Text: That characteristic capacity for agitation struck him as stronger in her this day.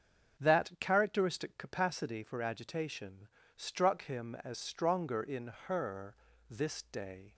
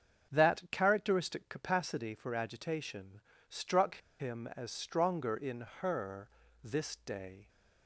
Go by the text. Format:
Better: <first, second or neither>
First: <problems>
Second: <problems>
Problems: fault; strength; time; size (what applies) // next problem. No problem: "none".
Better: first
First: starts louder than the rest; until 1.4 s; 7 dB // pauses between "agitation" and "struck"; slight; at 3.2 s; 0.28 s long // pauses between "her" and "this"; slight; at 6.1 s; 0.34 s long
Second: starts louder than the rest; until 1.4 s; 7 dB // pauses between "agitation" and "struck"; slight; at 3.2 s; 0.28 s long // pauses between "struck" and "him"; slight; at 3.9 s; 0.21 s long // pauses between "her" and "this"; slight; at 6.2 s; 0.34 s long